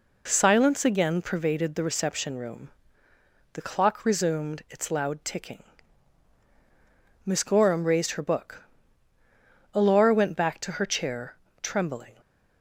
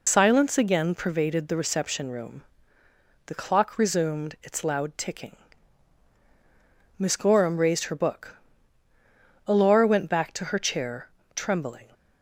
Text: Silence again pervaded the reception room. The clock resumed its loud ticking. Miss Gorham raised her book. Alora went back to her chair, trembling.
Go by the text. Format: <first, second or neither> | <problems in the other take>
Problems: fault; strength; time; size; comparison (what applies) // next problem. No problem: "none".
first | loses the start of "Silence"; at 0.0 s; 85 ms